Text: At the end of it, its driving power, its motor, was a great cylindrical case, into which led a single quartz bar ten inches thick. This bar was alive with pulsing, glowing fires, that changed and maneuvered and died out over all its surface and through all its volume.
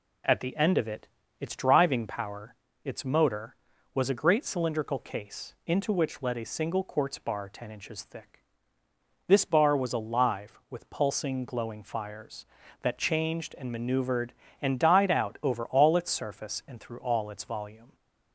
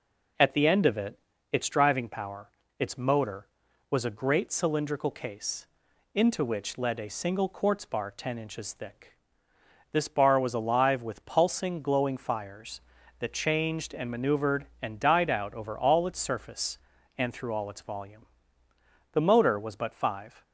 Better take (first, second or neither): first